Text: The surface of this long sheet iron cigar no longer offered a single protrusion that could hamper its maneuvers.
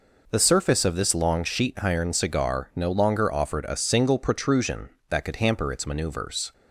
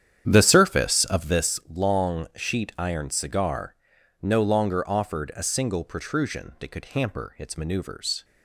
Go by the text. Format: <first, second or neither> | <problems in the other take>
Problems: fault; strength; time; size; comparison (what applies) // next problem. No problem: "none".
first | starts louder than the rest; strong; until 1.5 s; 9.5 dB // pauses between "cigar" and "no"; at 3.7 s; 0.44 s long